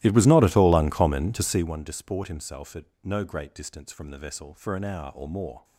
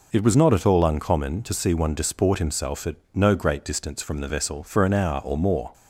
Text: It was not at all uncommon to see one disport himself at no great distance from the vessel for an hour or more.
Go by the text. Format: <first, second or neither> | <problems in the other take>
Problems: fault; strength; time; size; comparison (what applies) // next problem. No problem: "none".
second | starts louder than the rest; strong; until 1.7 s; 16 dB // pauses between "at" and "no"; slight; at 2.8 s; 0.18 s long; slight in the second